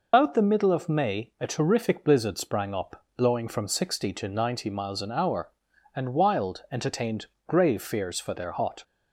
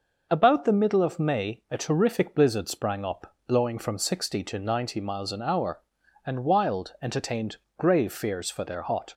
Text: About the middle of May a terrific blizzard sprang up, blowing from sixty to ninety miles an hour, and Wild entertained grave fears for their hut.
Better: second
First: loses the start of "About"; at 0.1 s; 140 ms // pauses between "entertained" and "grave"; slight; at 7.2 s; 0.20 s long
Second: pauses between "entertained" and "grave"; slight; at 7.5 s; 0.20 s long

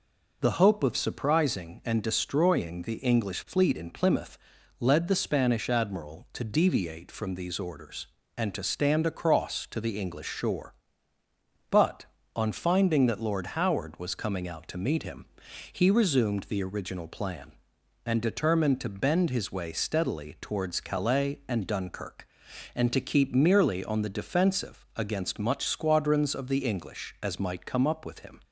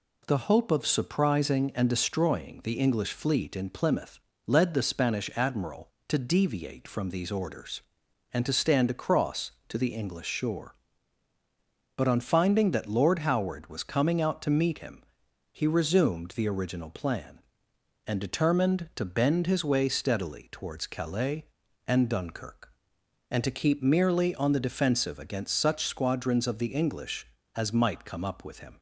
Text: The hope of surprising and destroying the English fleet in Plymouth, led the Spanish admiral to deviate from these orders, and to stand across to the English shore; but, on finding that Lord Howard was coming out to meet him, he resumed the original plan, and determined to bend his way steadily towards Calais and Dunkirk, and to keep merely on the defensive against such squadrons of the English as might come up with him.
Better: second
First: says "much" for "such"; at 25.3 s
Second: none

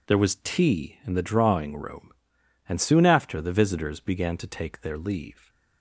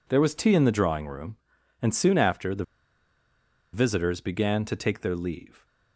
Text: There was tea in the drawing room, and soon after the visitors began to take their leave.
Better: first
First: none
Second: pauses between "the" and "visitors"; at 2.6 s; 1.1 s long

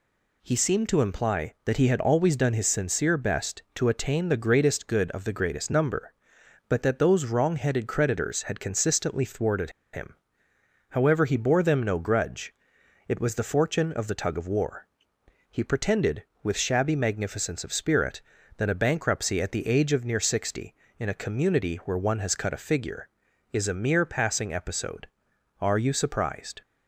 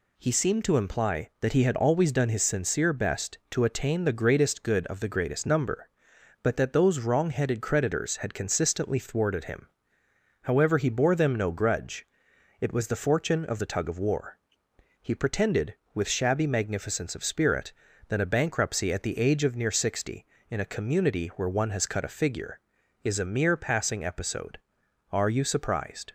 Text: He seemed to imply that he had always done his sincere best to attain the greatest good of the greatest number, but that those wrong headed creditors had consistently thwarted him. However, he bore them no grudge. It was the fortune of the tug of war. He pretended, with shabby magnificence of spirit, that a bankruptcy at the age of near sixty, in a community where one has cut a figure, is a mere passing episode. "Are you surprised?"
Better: second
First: pauses between "thwarted" and "him"; slight; at 9.7 s; 0.21 s long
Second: none

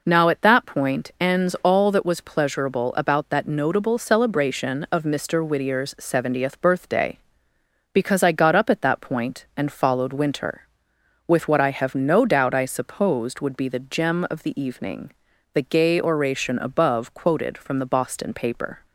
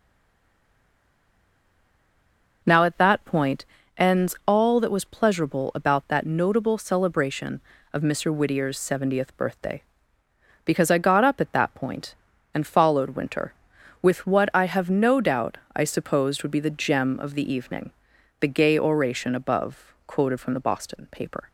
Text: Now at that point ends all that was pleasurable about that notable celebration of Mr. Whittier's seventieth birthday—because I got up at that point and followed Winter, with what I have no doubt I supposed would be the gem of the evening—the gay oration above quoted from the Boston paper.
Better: first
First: none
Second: stays silent before the first word; strong; until 2.6 s; 2.6 s long // pauses between "point" and "ends"; slight; at 3.6 s; 0.32 s long // pauses between "doubt" and "I"; slight; at 15.5 s; 0.18 s long

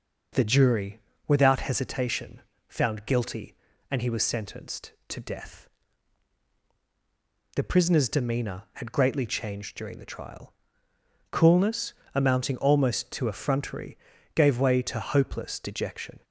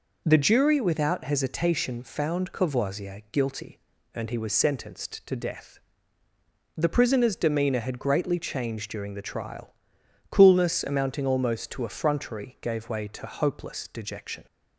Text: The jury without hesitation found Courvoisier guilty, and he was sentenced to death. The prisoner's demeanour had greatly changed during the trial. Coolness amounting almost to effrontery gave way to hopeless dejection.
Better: second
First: pauses between "jury" and "without"; slight; at 0.9 s; 0.30 s long // pauses between "hesitation" and "found"; slight; at 2.4 s; 0.26 s long // skips "Courvoisier"; at 3.0 s // pauses between "Coolness" and "amounting"; slight; at 11.9 s; 0.22 s long // pauses between "effrontery" and "gave"; at 13.9 s; 0.38 s long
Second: none

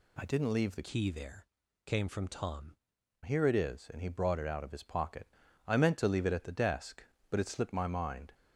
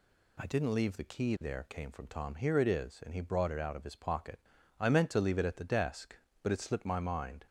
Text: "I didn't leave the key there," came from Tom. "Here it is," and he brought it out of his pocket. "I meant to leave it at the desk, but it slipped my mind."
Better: second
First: changes voice from "key" to "Tom"; from 0.8 to 2.7 s; 1.9 s long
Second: none

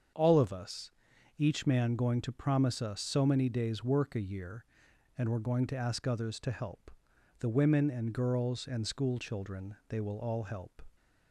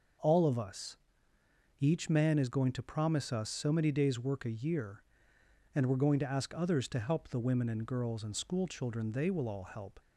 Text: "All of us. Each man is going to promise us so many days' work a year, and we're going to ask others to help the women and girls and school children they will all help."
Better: second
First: starts louder than the rest; until 1.6 s; 7 dB // skips "is"; at 1.9 s // pauses between "help" and "the"; noticeable; at 6.8 s; 0.50 s long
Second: none

